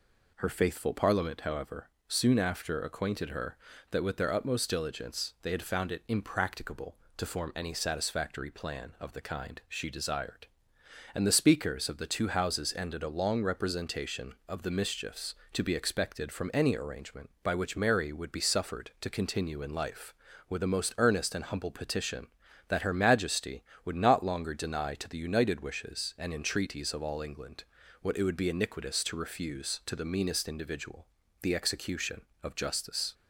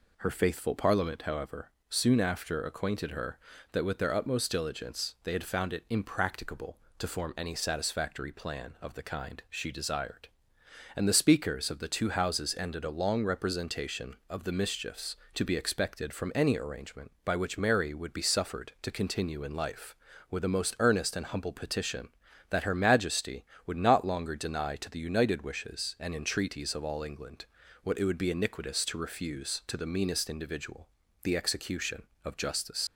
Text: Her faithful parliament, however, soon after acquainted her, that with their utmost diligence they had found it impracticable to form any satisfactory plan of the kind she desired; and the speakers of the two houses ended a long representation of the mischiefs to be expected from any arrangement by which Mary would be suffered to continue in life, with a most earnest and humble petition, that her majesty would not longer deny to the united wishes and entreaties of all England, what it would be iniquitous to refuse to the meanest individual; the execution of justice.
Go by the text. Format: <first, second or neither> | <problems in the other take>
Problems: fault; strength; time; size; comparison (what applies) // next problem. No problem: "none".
first | leaves "justice" unfinished; at 32.8 s; 75 ms